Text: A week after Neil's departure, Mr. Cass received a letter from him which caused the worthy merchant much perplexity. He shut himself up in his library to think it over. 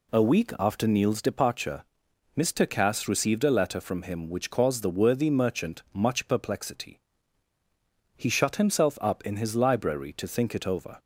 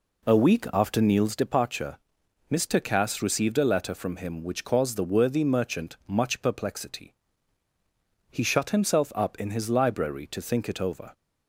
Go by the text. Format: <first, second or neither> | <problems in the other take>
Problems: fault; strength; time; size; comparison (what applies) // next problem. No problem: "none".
first | starts louder than the rest; slight; until 1.4 s; 3.5 dB